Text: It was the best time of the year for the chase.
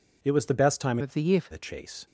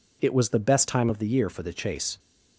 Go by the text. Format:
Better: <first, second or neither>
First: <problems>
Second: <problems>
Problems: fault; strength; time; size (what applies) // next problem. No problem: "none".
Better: second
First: changes voice from "of" to "for"; from 1.0 to 1.5 s; 0.5 s long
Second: none